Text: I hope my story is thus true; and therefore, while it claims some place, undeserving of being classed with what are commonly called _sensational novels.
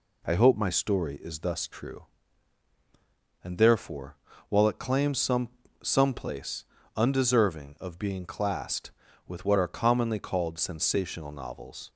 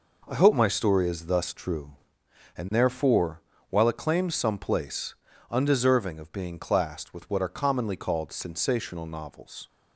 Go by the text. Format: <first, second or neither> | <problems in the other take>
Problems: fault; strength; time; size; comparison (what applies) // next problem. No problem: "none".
second | says "some" twice; at 5.8 s